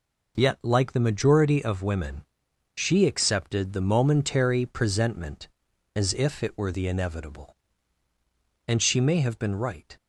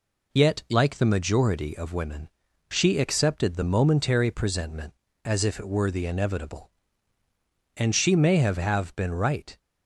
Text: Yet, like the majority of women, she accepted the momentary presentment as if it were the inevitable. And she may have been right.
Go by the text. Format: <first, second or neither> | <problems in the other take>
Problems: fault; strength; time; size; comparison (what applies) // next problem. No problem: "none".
first | says "have" twice; at 8.5 s